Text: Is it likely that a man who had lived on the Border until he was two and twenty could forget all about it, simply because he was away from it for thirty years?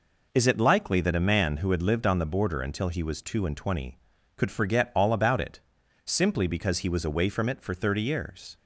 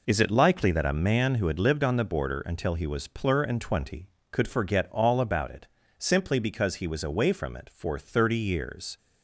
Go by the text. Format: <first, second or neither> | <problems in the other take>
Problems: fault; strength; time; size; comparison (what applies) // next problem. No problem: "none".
first | says "plur" for "two"; at 3.0 s